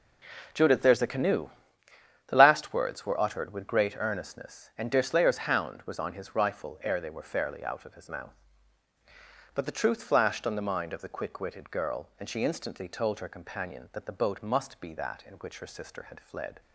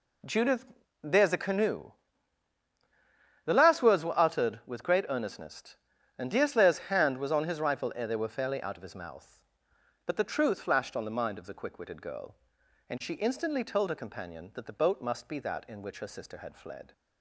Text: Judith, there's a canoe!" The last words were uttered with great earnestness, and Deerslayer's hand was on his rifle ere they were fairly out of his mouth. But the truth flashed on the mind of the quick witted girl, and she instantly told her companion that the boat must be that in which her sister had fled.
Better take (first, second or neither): second